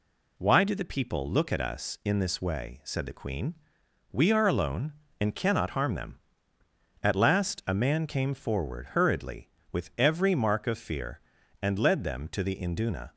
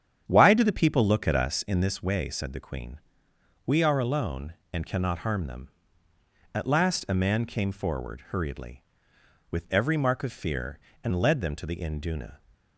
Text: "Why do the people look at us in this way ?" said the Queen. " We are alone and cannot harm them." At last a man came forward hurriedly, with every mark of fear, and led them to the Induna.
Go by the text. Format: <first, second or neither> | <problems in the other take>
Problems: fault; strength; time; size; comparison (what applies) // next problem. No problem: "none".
first | starts louder than the rest; strong; until 1.6 s; 8 dB